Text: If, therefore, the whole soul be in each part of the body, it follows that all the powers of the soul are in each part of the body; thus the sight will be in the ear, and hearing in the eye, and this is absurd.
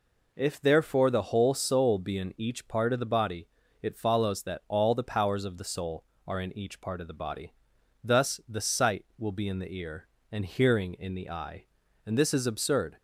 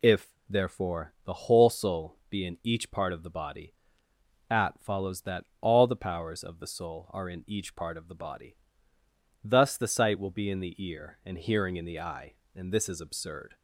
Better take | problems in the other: first | says "at" for "it"; at 4.5 s // pauses between "that" and "all"; slight; at 5.4 s; 0.16 s long

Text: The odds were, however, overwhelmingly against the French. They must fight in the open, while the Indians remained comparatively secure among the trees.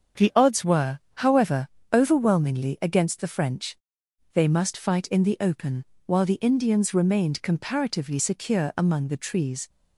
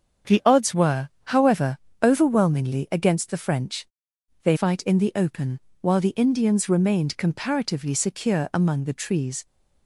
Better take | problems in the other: first | starts louder than the rest; strong; until 1.4 s; 7 dB; also in the first // skips "must"; at 4.5 s

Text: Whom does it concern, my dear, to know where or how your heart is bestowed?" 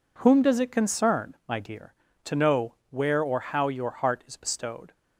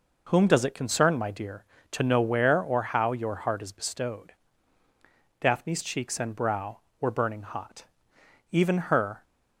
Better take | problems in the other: first | goes on to say "Daphne's cheeks and brow were burning hot even her"; strong; from 5.3 s on; 3.8 s long

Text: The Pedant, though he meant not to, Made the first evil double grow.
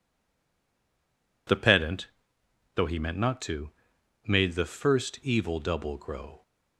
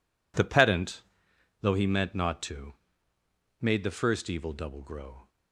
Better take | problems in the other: second | stays silent before the first word; noticeable; until 1.4 s; 1.4 s long

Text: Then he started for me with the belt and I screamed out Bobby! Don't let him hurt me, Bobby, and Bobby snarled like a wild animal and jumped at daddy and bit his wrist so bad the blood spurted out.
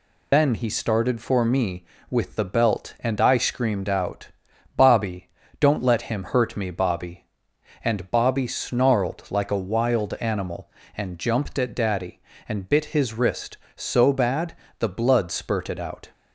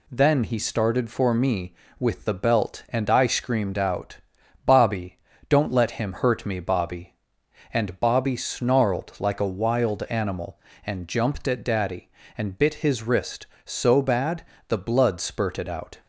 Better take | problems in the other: second | loses the start of "Then"; at 0.3 s; 145 ms // pauses between "out" and "Bobby"; noticeable; at 4.2 s; 0.48 s long; noticeable in the second // pauses between "bad" and "the"; slight; at 14.5 s; 0.24 s long; slight in the second

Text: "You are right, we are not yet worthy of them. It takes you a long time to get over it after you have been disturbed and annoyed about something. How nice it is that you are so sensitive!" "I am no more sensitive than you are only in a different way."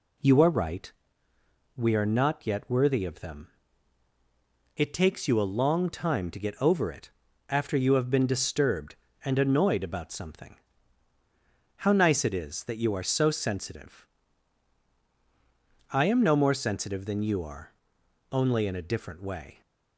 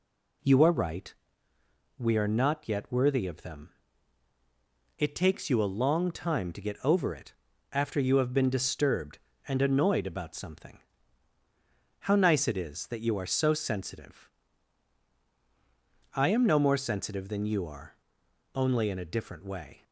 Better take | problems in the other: neither | pauses between "it" and "after"; the same in both // pauses between "are" and "only"; noticeable; the same in both

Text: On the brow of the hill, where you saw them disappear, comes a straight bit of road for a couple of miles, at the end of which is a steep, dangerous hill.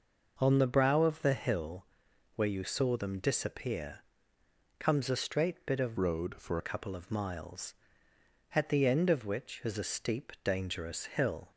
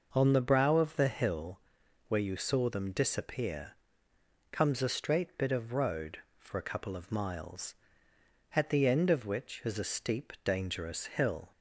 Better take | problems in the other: second | changes voice from "road" to "for"; from 5.9 to 6.5 s; 0.6 s long

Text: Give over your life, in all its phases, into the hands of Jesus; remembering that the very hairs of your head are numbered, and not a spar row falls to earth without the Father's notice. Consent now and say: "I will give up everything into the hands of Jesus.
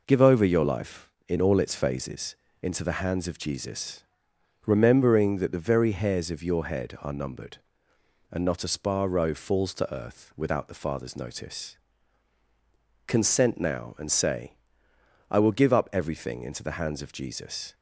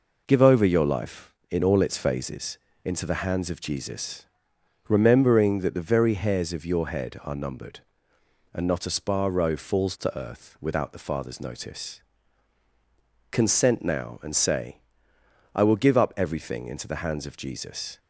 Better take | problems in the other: neither | none

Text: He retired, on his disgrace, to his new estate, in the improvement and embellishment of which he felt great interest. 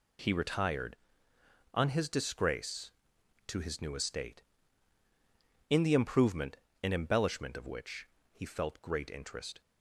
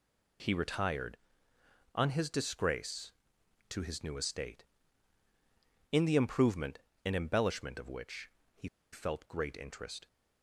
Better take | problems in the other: first | pauses between "which" and "he"; slight; at 8.3 s; 0.24 s long; slight in the first // pauses between "he" and "felt"; slight; at 8.6 s; 0.25 s long

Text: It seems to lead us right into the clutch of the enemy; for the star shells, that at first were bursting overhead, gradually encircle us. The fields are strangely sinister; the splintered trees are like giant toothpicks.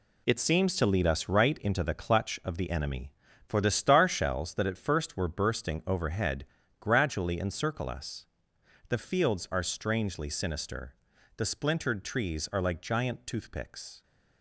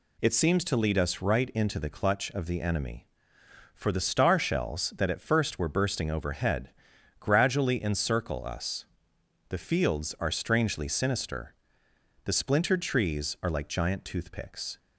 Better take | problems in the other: second | gets quieter; strong; throughout; 8.5 dB

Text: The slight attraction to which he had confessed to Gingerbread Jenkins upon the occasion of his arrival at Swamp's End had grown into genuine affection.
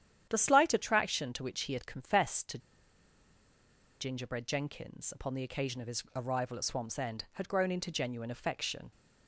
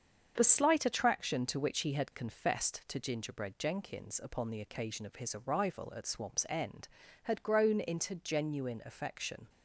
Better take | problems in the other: second | starts louder than the rest; strong; until 1.3 s; 9.5 dB; also in the second // pauses between "to" and "Gingerbread"; strong; at 2.5 s; 1.4 s long

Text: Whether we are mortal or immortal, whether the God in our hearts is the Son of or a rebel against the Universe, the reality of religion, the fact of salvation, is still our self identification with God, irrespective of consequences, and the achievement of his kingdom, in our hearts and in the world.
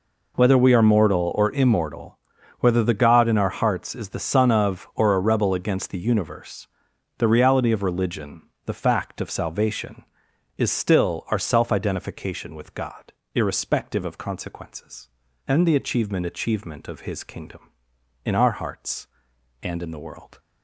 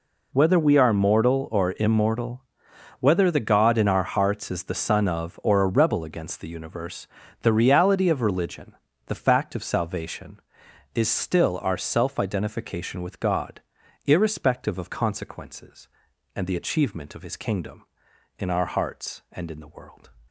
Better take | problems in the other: second | says "achievement" twice; at 16.2 s

